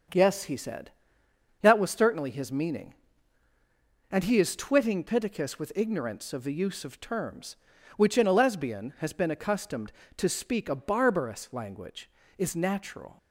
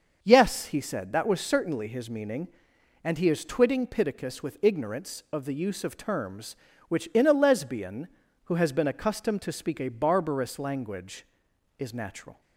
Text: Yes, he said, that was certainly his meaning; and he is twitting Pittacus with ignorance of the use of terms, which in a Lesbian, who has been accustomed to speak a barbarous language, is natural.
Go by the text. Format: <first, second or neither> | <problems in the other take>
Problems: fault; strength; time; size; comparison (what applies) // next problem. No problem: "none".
second | starts louder than the rest; until 1.8 s; 7 dB; also in the second // skips "who"; at 8.9 s